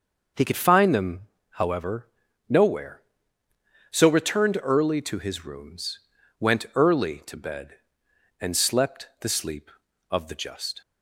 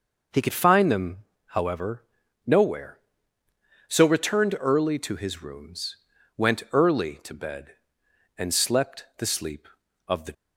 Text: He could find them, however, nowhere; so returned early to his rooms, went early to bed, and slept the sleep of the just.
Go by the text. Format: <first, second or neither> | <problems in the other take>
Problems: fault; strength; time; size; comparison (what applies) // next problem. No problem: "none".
first | stops before "just"; at 10.3 s